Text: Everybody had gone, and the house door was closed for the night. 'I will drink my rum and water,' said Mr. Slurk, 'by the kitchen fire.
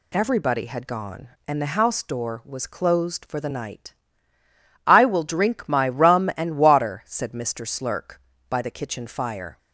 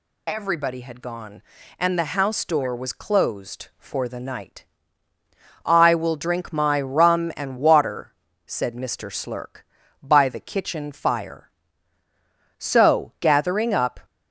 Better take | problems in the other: first | goes on to say "So gathering up"; from 12.5 s on; 1.4 s long

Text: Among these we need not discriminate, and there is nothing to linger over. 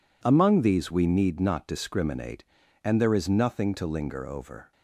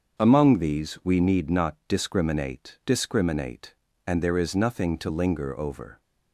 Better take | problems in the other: first | starts louder than the rest; until 1.2 s; 6.5 dB // says "discriminate" twice; at 2.8 s

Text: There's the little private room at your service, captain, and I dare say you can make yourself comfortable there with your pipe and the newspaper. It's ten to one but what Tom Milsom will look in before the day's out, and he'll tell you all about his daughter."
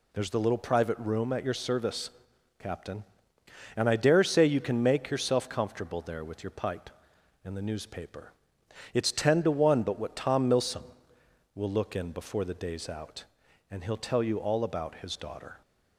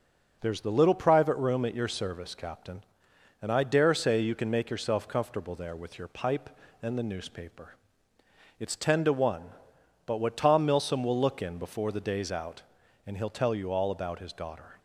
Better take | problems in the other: neither | none

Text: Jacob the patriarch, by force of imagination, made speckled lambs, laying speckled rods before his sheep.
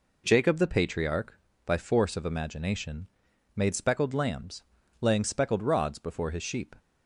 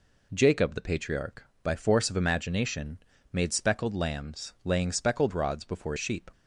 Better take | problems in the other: first | skips "his"; at 5.9 s

